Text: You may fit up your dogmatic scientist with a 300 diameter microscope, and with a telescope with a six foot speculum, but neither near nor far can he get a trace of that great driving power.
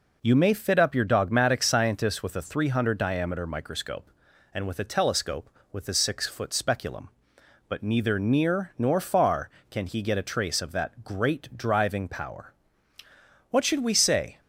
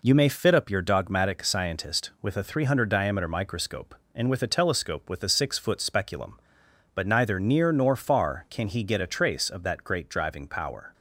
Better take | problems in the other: second | goes on to say "What should we say"; noticeable; from 13.4 s on; 0.90 s long

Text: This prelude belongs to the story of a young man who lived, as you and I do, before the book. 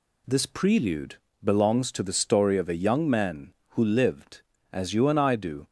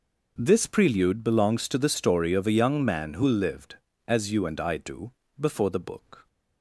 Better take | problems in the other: second | pauses between "prelude" and "belongs"; slight; at 1.1 s; 0.26 s long // stops before "before the book"; at 5.6 s

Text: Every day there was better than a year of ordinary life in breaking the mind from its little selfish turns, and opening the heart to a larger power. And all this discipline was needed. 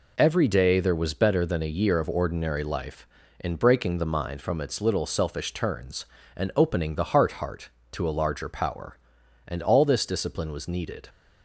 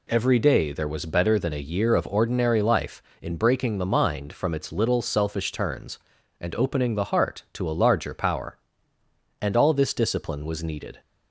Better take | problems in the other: second | says "heart" twice; at 7.3 s

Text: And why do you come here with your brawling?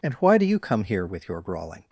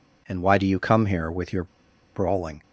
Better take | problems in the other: first | pauses between "your" and "brawling"; noticeable; at 1.6 s; 0.49 s long

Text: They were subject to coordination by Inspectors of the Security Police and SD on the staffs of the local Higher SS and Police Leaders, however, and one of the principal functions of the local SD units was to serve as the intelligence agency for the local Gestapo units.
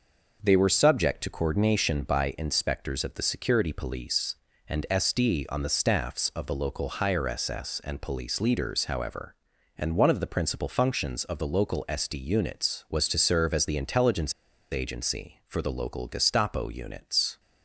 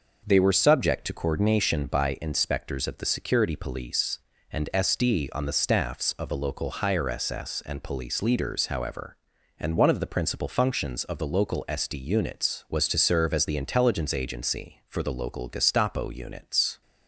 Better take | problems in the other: second | pauses between "intelligence" and "agency"; at 14.3 s; 0.39 s long

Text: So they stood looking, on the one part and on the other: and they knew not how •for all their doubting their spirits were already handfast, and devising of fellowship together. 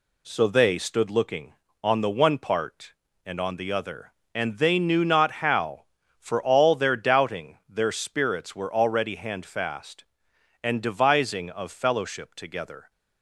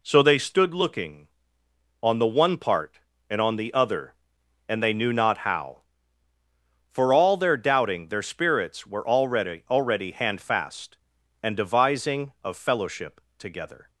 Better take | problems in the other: first | says "already" twice; at 9.6 s // pauses between "fellowship" and "together"; slight; at 13.1 s; 0.18 s long

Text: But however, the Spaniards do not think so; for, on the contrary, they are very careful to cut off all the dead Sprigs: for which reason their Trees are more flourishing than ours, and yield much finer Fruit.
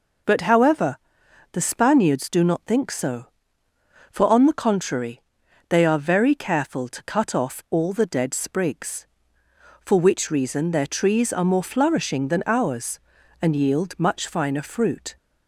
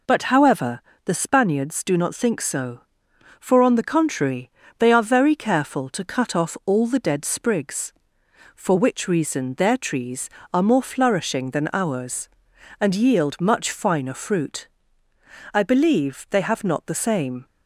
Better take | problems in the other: first | goes on to say "I believe they have not the same"; strong; from 15.5 s on; 1.9 s long

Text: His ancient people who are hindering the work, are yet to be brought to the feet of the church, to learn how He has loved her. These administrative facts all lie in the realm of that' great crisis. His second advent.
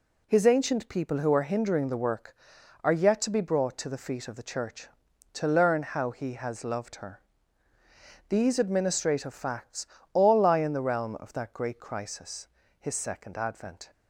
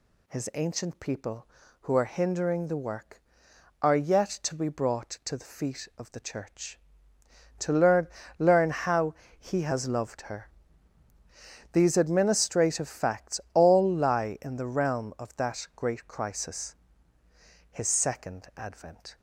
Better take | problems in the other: first | says "learn" twice; at 8.3 s // pauses between "how" and "He"; slight; at 9.1 s; 0.24 s long // pauses between "facts" and "all"; slight; at 13.3 s; 0.16 s long; slight in the first

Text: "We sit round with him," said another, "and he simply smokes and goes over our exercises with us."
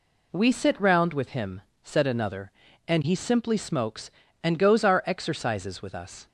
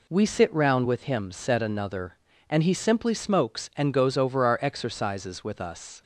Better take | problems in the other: second | skips "over"; at 4.8 s

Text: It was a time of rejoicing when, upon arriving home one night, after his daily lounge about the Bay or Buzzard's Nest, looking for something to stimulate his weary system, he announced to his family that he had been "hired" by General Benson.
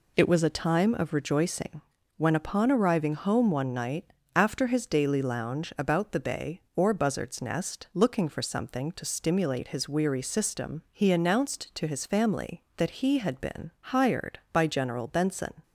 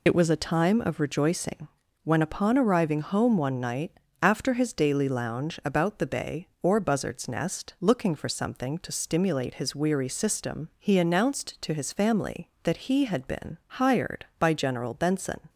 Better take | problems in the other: first | loses the start of "It"; at 0.0 s; 30 ms // pauses between "rejoicing" and "when"; slight; at 1.6 s; 0.36 s long; slight in the first

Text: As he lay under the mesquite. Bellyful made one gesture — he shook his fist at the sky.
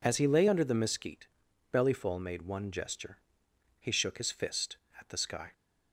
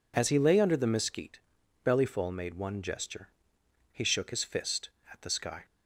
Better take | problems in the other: neither | none

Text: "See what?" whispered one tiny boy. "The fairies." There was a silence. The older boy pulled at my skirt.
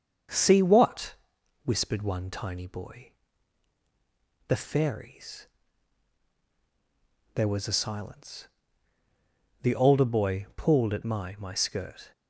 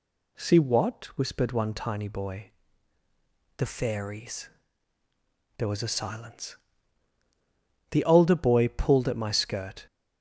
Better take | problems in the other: second | starts louder than the rest; until 1.7 s; 6.5 dB // says "my" twice; at 11.3 s

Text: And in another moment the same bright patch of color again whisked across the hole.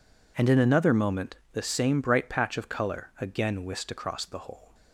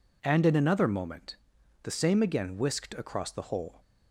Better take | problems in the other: first | pauses between "moment" and "the"; noticeable; at 1.3 s; 0.46 s long; slight in the first // skips "bright patch of color"; at 2.2 s

